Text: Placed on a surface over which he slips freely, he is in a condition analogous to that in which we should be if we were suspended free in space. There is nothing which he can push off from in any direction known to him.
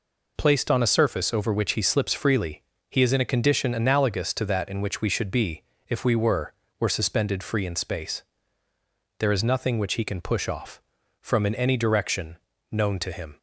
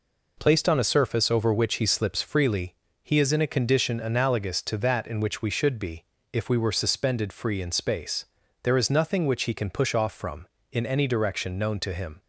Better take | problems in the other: second | pauses between "be" and "if"; slight; at 5.6 s; 0.24 s long; slight in the second // says "were" twice; at 6.7 s // pauses between "direction" and "known"; slight; at 12.3 s; 0.34 s long

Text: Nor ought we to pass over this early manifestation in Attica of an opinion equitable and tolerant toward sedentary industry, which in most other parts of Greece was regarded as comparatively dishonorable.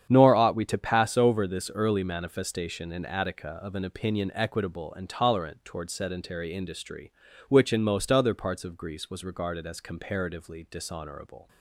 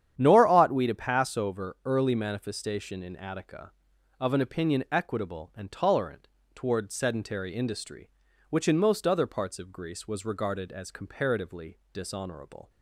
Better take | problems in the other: first | starts louder than the rest; strong; until 1.1 s; 9.5 dB; strong in the first // skips "this"; at 1.7 s // pauses between "tolerant" and "toward"; slight; at 6.2 s; 0.26 s long

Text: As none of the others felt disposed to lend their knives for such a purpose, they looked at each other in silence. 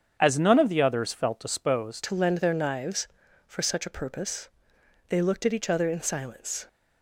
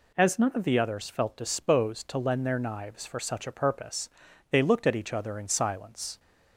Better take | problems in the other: second | starts louder than the rest; strong; until 1.2 s; 7.5 dB // changes voice at "to"; from 2.0 s on; 4.6 s long

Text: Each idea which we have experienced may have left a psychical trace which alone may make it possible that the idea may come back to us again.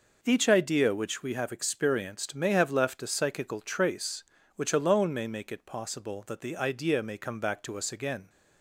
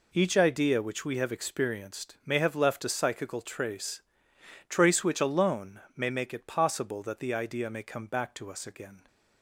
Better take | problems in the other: first | says "trace" twice; at 4.6 s // pauses between "alone" and "may"; slight; at 5.7 s; 0.16 s long

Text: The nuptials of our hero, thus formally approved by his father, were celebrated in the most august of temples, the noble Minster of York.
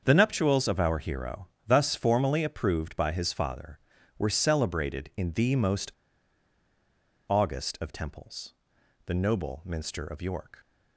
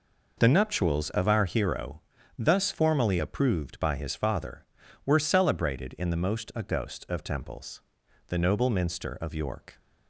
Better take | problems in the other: second | starts louder than the rest; until 1.0 s; 7 dB // pauses between "most" and "august"; strong; at 5.9 s; 1.3 s long

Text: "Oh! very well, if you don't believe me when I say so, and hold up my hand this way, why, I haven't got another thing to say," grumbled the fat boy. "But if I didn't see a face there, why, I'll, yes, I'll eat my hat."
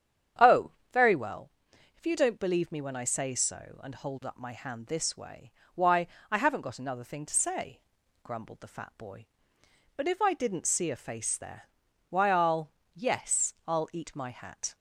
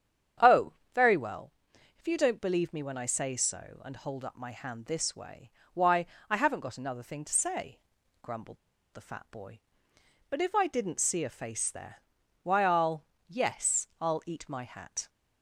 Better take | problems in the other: first | starts louder than the rest; strong; until 2.1 s; 8.5 dB; strong in the first // pauses between "grumbled" and "the"; at 8.5 s; 0.36 s long

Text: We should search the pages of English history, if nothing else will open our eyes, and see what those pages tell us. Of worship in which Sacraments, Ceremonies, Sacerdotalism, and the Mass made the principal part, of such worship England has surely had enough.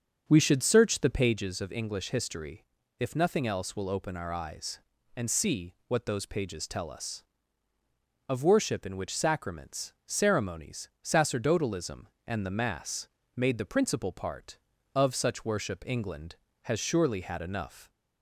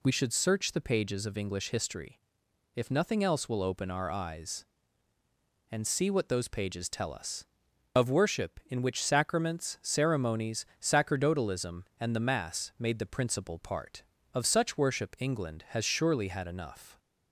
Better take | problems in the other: second | starts louder than the rest; until 1.4 s; 7 dB // pauses between "Mass" and "made"; slight; at 13.0 s; 0.30 s long

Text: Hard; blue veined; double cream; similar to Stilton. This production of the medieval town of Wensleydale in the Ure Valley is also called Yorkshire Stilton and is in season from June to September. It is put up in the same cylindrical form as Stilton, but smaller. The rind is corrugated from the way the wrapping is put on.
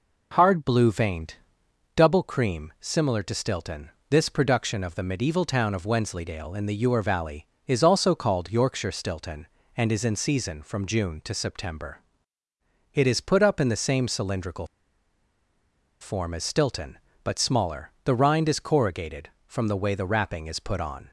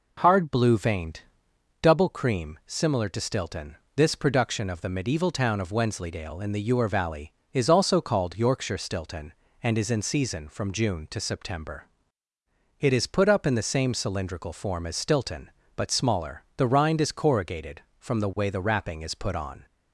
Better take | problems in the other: second | pauses between "cylindrical" and "form"; strong; at 14.6 s; 1.3 s long

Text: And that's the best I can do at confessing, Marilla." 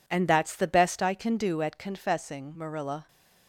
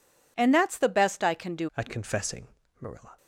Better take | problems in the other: first | changes voice at "at"; from 1.7 s on; 1.4 s long

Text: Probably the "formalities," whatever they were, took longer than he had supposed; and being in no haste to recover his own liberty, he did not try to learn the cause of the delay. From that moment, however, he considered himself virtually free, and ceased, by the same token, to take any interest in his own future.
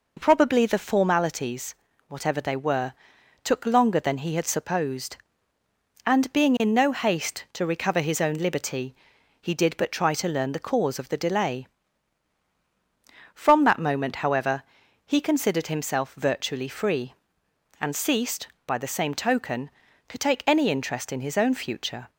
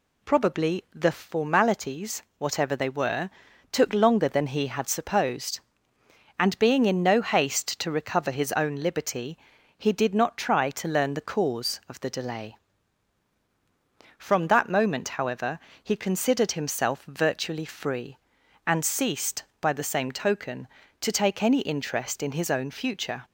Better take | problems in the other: second | says "but" for "not"; at 9.7 s

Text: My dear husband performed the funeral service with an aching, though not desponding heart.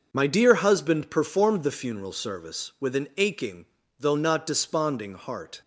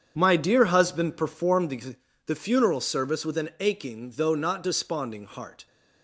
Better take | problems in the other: first | starts louder than the rest; strong; until 1.1 s; 7.5 dB; also in the first // says "the" twice; at 2.2 s

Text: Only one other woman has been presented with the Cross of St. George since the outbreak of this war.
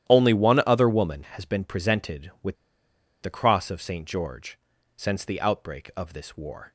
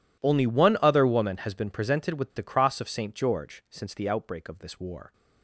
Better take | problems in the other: second | starts louder than the rest; strong; until 1.1 s; 11.5 dB // pauses between "with" and "the"; noticeable; at 2.5 s; 0.66 s long // pauses between "George" and "since"; at 4.5 s; 0.40 s long

